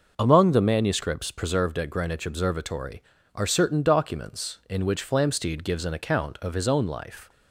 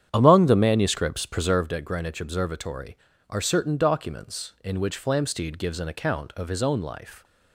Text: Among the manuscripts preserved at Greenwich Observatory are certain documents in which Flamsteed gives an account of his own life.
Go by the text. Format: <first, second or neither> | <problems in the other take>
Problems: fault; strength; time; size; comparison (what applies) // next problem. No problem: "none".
first | starts louder than the rest; strong; until 1.8 s; 9 dB